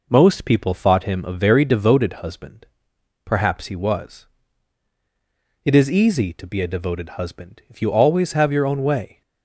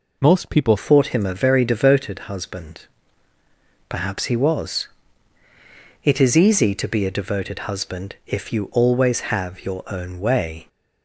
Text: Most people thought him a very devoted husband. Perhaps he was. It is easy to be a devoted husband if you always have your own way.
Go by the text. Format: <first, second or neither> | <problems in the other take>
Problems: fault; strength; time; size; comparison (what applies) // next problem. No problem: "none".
first | changes voice at "thought"; from 0.7 s on; 9.9 s long